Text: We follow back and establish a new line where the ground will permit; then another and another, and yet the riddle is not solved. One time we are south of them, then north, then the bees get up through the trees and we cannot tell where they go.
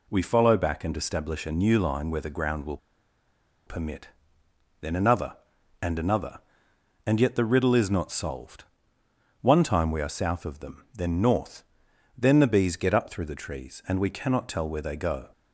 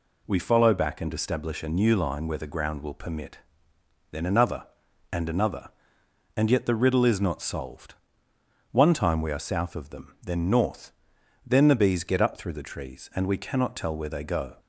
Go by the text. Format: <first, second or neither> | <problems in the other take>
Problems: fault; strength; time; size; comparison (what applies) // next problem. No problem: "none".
second | pauses between "will" and "permit"; noticeable; at 2.7 s; 0.89 s long